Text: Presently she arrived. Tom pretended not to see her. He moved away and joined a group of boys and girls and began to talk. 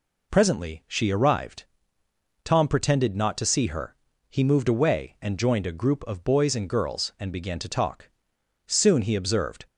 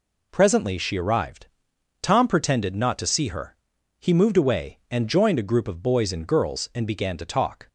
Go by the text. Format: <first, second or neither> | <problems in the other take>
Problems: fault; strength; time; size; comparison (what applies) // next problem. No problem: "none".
second | goes on to say "Soon he observed"; noticeable; from 8.6 s on; 0.98 s long